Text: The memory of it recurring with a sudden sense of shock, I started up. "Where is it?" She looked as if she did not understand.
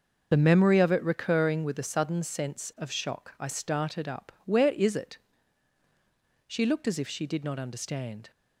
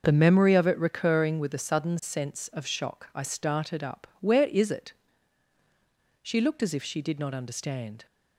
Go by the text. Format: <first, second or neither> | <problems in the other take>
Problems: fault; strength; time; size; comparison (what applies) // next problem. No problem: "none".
second | loses the start of "The"; at 0.3 s; 25 ms // starts louder than the rest; noticeable; until 1.3 s; 6 dB